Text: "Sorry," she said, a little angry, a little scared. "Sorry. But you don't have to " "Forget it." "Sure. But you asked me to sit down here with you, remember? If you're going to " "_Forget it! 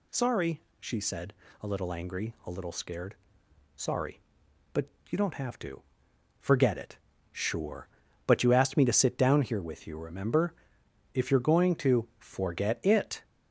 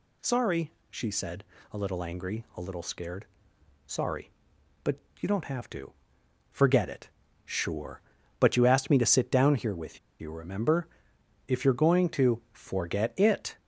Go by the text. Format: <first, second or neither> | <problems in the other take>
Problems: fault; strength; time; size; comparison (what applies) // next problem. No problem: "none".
first | pauses between "But" and "you"; slight; at 4.9 s; 0.22 s long; slight in the first // pauses between "with" and "you"; slight; at 9.9 s; 0.22 s long